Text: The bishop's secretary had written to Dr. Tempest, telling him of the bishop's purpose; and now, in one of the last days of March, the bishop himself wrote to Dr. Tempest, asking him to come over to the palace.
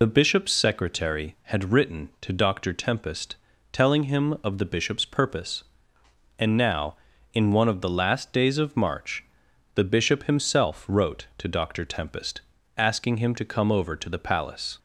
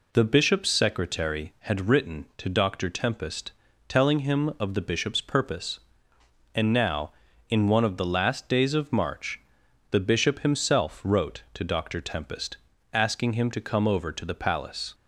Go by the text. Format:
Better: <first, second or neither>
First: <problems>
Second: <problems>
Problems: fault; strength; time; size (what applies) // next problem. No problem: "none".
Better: second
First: loses the start of "The"; at 0.0 s; 55 ms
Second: none